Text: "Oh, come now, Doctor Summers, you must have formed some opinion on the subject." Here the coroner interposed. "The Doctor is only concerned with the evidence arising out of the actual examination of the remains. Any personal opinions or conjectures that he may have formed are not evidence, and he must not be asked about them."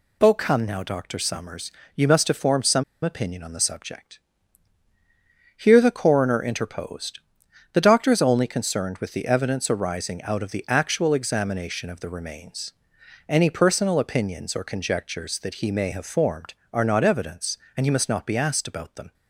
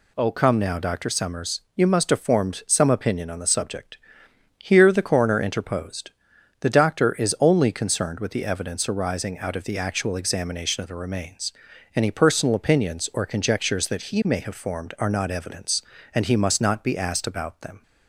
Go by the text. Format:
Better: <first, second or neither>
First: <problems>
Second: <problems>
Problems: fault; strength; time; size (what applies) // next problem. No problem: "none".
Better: second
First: pauses between "some" and "opinion"; slight; at 2.8 s; 0.21 s long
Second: none